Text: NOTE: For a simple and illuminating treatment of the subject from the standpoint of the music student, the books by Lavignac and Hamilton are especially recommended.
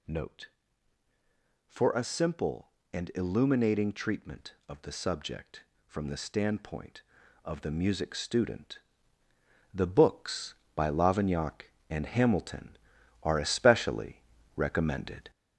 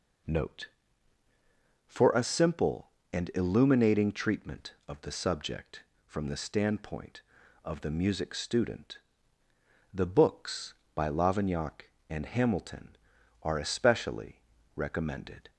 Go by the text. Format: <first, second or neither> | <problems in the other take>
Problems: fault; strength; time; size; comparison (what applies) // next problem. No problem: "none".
second | gets louder; noticeable; throughout; 5.5 dB // pauses between "especially" and "recommended"; slight; at 14.2 s; 0.36 s long; slight in the second